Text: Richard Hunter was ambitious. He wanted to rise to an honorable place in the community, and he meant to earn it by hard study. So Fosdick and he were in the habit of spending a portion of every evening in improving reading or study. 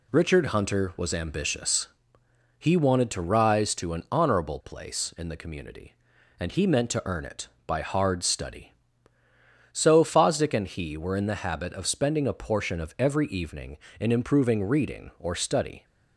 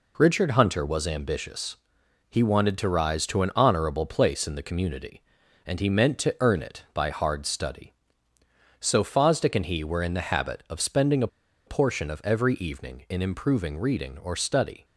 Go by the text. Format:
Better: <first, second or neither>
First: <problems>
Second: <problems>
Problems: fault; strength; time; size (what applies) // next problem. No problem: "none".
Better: first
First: none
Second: pauses between "a" and "portion"; at 11.2 s; 0.38 s long